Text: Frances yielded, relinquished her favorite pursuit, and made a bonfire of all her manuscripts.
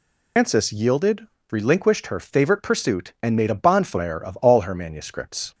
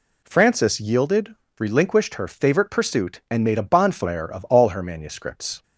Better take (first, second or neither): second